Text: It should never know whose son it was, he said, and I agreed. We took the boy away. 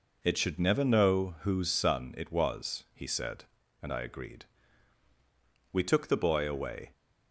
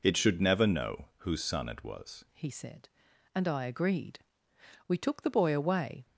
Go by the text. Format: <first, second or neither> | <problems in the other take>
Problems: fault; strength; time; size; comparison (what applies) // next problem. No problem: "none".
first | changes voice at "he"; from 2.3 s on; 3.7 s long